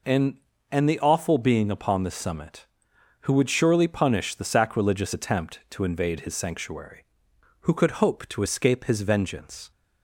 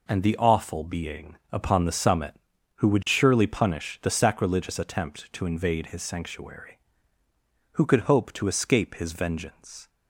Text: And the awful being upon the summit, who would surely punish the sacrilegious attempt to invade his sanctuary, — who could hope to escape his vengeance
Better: second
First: says "And" twice; at 0.7 s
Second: none

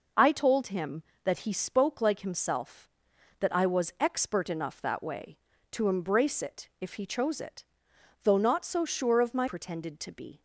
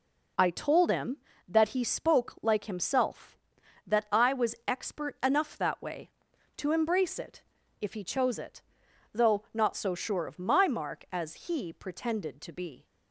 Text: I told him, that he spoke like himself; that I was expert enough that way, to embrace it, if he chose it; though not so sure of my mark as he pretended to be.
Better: second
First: skips "mark as he"; at 9.4 s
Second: none

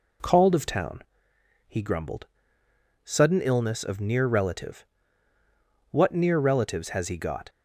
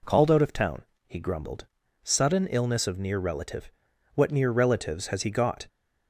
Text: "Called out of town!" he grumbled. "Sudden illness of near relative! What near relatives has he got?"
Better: second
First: skips "out"; at 0.5 s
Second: none

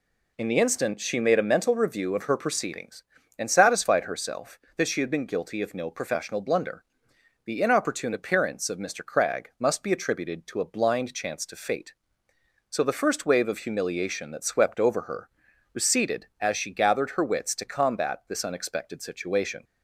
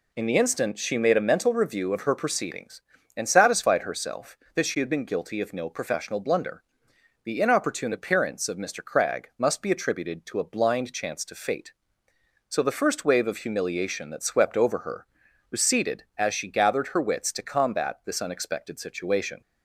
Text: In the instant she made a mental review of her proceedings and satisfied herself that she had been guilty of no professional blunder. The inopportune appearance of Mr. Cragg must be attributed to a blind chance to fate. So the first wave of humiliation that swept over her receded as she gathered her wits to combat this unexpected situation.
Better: neither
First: pauses between "her" and "receded"; at 15.2 s; 0.42 s long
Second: pauses between "her" and "receded"; at 15.0 s; 0.42 s long

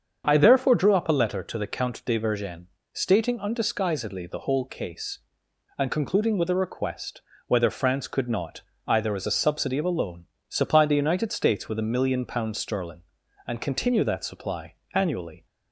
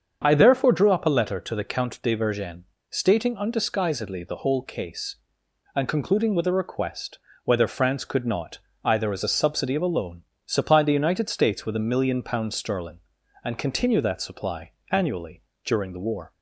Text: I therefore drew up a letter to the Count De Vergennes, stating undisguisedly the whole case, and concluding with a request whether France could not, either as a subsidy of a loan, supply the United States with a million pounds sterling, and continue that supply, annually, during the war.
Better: second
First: starts louder than the rest; until 1.2 s; 7 dB // pauses between "request" and "whether"; slight; at 7.2 s; 0.24 s long // stops before "during the war"; at 15.4 s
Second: starts louder than the rest; until 1.2 s; 7 dB // pauses between "request" and "whether"; slight; at 7.1 s; 0.24 s long

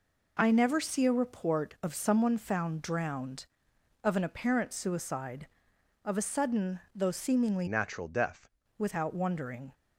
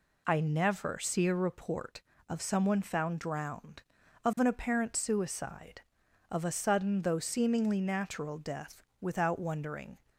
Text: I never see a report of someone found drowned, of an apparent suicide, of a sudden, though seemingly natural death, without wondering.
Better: second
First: changes voice from "natural" to "death"; from 7.6 to 8.5 s; 0.9 s long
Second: none

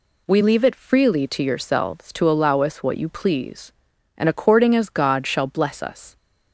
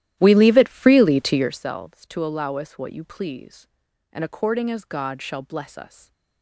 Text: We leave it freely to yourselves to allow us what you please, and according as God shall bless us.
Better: first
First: none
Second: starts louder than the rest; strong; until 1.6 s; 13 dB // stays silent after the last word; slight; from 5.8 s on; 0.6 s long

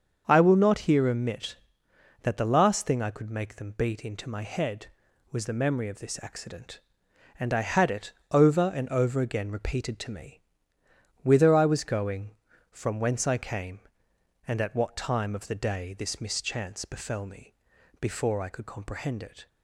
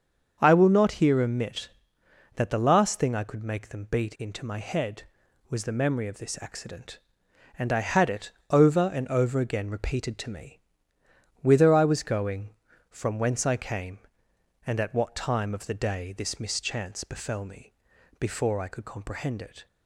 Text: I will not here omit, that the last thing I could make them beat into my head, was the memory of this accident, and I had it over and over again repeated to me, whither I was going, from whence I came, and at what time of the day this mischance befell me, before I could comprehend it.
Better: neither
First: starts louder than the rest; until 1.2 s; 7 dB // pauses between "it" and "over"; slight; at 8.1 s; 0.20 s long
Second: starts louder than the rest; until 1.4 s; 7 dB // pauses between "it" and "over"; slight; at 8.3 s; 0.20 s long

